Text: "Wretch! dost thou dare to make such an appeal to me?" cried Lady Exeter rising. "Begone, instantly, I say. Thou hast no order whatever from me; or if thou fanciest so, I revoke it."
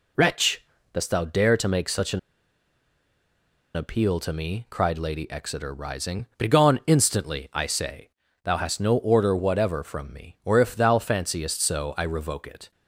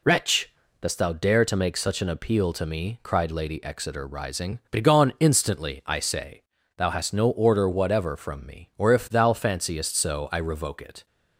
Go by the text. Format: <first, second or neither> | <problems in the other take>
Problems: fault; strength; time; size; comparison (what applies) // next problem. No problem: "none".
second | pauses between "an" and "appeal"; strong; at 2.1 s; 1.5 s long